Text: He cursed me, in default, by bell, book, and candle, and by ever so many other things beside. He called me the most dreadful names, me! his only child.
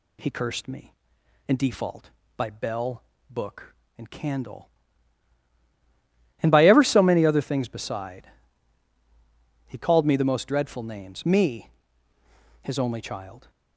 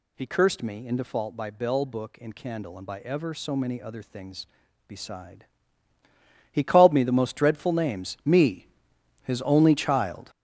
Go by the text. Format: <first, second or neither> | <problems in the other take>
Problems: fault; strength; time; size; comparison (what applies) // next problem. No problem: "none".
first | gets louder; strong; throughout; 9.5 dB